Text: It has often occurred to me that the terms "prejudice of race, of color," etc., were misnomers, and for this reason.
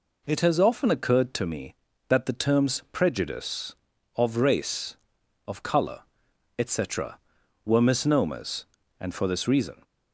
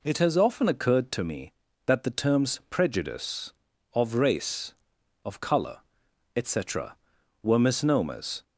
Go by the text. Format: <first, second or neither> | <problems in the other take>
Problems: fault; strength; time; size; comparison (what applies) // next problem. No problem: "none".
first | stops before "and for this reason"; at 8.4 s